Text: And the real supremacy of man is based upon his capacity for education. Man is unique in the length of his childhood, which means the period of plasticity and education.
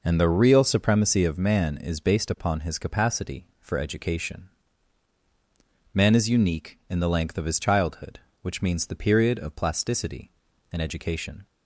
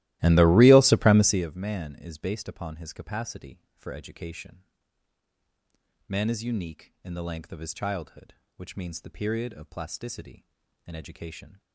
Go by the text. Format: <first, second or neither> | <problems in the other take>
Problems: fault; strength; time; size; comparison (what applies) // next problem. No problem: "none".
first | starts louder than the rest; strong; until 1.5 s; 16.5 dB